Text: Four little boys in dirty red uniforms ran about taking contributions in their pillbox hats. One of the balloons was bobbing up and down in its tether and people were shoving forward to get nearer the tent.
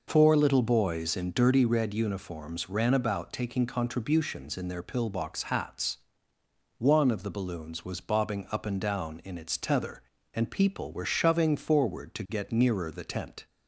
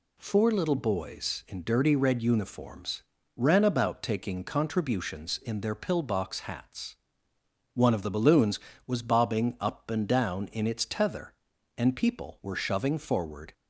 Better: first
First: none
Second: pauses between "uniforms" and "ran"; slight; at 3.0 s; 0.34 s long // stops before "to get nearer the tent"; at 13.5 s

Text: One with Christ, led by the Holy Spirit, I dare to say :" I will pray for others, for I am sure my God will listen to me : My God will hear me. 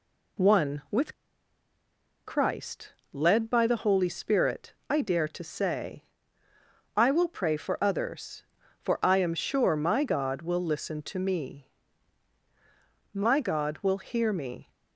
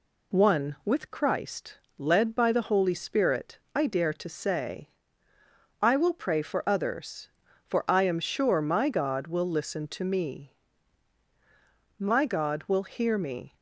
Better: second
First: pauses between "with" and "Christ"; at 1.1 s; 1.1 s long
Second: none

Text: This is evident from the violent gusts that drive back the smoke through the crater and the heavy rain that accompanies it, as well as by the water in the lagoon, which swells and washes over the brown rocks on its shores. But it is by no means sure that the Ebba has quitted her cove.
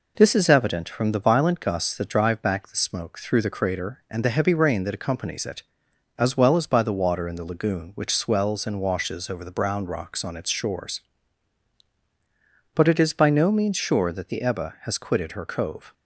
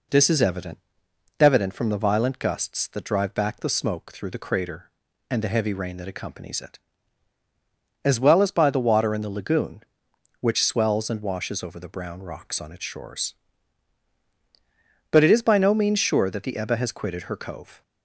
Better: first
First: none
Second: says "evident" twice; at 1.3 s

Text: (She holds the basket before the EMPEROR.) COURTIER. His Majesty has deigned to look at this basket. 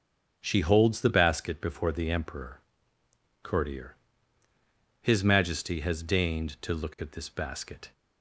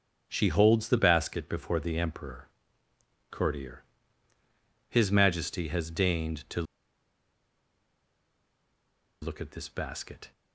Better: first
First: starts louder than the rest; until 1.4 s; 6 dB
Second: starts louder than the rest; until 1.2 s; 6 dB // pauses between "to" and "look"; strong; at 6.6 s; 2.5 s long

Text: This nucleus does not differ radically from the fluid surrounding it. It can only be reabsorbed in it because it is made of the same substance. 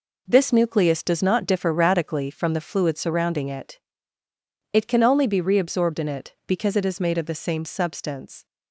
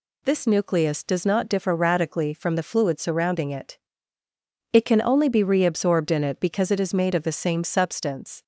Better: second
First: gets quieter; strong; throughout; 8 dB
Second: none

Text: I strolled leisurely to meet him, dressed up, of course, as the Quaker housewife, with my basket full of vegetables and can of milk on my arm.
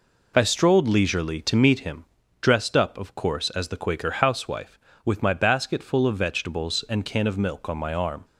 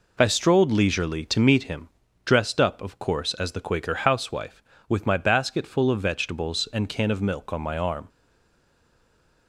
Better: first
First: none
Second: stays silent after the last word; noticeable; from 8.0 s on; 1.4 s long

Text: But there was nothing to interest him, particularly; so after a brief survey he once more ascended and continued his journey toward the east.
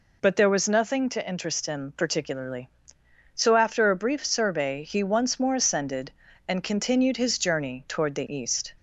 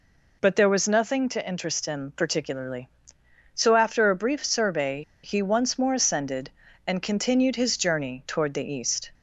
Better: first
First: none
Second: pauses between "survey" and "he"; slight; at 5.0 s; 0.22 s long

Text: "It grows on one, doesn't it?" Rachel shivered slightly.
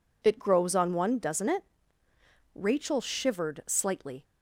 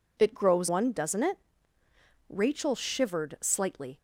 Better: first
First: none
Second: skips "on"; at 0.6 s

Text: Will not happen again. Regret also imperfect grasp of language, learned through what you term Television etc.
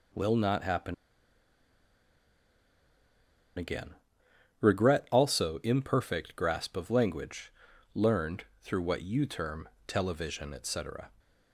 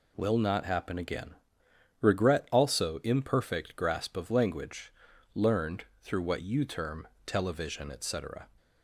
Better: second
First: pauses between "happen" and "again"; strong; at 0.9 s; 2.6 s long // pauses between "learned" and "through"; slight; at 8.4 s; 0.18 s long // pauses between "term" and "Television"; slight; at 9.6 s; 0.20 s long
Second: pauses between "learned" and "through"; slight; at 5.8 s; 0.18 s long // pauses between "term" and "Television"; slight; at 7.0 s; 0.20 s long

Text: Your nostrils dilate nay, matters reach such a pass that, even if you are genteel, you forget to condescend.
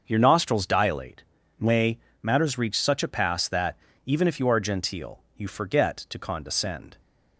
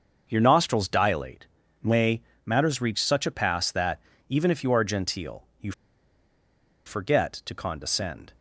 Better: first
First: starts louder than the rest; until 1.0 s; 6.5 dB // pauses between "dilate" and "nay"; slight; at 1.2 s; 0.36 s long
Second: starts louder than the rest; until 1.3 s; 6.5 dB // pauses between "dilate" and "nay"; slight; at 1.4 s; 0.36 s long // pauses between "you" and "forget"; at 5.7 s; 1.1 s long

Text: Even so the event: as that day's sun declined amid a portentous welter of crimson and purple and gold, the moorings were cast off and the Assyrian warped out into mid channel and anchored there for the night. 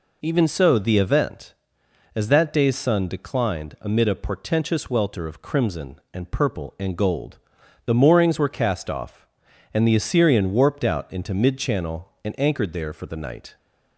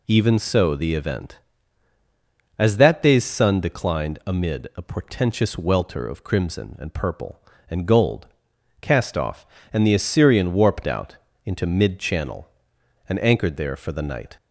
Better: first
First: none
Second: skips "the moorings were"; at 8.5 s // pauses between "out" and "into"; slight; at 11.1 s; 0.30 s long

